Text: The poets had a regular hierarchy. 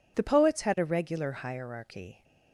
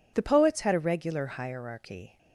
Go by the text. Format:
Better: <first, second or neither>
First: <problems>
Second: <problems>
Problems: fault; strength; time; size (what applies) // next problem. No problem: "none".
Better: neither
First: none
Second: none